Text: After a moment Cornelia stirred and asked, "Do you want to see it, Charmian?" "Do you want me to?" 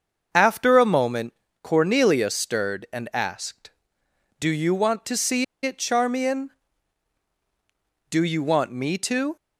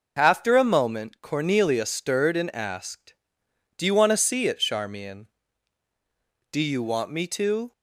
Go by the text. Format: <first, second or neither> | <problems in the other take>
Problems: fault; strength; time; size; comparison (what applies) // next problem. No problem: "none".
second | starts louder than the rest; until 1.3 s; 6.5 dB // pauses between "moment" and "Cornelia"; slight; at 1.3 s; 0.28 s long // pauses between "see" and "it"; slight; at 5.4 s; 0.19 s long